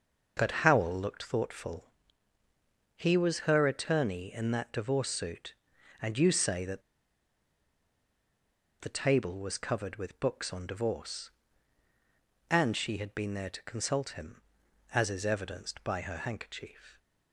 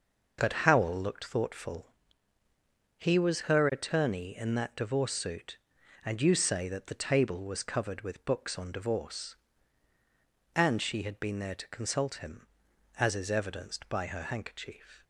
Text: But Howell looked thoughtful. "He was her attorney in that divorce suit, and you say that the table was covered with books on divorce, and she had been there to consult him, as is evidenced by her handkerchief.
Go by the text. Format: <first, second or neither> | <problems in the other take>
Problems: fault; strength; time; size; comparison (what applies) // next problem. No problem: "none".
second | pauses between "that" and "the"; strong; at 6.8 s; 2.0 s long